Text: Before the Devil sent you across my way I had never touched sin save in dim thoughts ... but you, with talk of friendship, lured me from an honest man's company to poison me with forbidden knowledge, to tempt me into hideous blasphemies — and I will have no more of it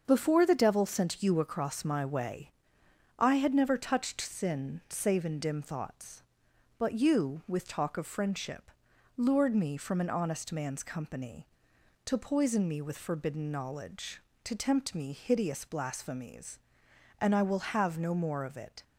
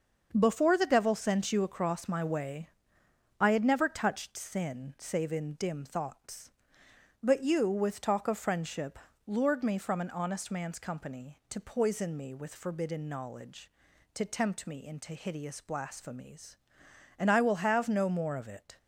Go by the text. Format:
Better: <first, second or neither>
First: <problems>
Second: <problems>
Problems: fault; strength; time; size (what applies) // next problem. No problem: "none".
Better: second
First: starts louder than the rest; until 1.0 s; 7 dB // pauses between "way" and "I"; noticeable; at 2.5 s; 0.66 s long // skips "into"; at 15.1 s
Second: starts louder than the rest; until 1.3 s; 6.5 dB // pauses between "way" and "I"; noticeable; at 2.6 s; 0.68 s long